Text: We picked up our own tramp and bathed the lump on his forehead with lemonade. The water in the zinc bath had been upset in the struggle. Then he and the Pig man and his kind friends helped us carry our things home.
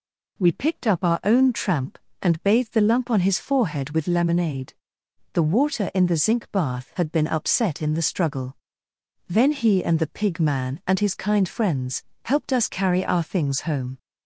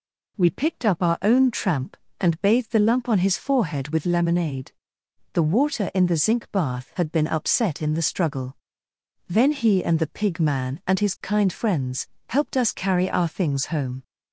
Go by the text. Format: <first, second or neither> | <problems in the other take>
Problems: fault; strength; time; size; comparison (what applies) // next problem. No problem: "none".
neither | pauses between "friends" and "helped"; slight; the same in both